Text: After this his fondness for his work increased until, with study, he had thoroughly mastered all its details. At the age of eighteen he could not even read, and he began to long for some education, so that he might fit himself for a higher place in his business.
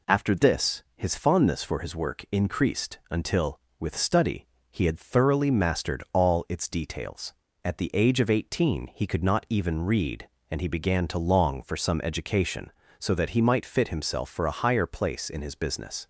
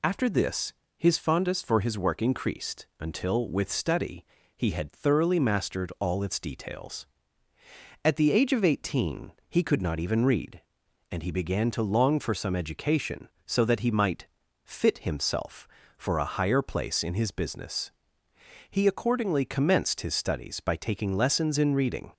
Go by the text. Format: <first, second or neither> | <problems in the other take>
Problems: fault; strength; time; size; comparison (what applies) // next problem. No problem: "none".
first | pauses between "this" and "his"; slight; at 0.7 s; 0.24 s long // pauses between "eighteen" and "he"; slight; at 9.3 s; 0.16 s long // pauses between "might" and "fit"; at 14.2 s; 0.38 s long // goes on to say "He accordingly commenced his studies by taking lessons in reading"; strong; from 18.6 s on; 3.4 s long